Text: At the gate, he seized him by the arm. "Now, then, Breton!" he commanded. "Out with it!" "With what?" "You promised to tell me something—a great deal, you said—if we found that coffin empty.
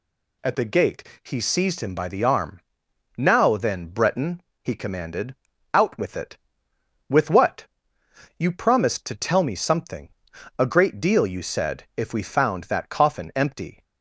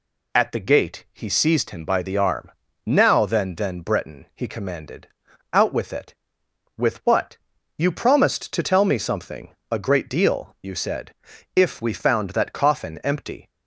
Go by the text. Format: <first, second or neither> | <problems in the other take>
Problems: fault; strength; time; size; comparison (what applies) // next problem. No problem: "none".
first | says "then" twice; at 3.5 s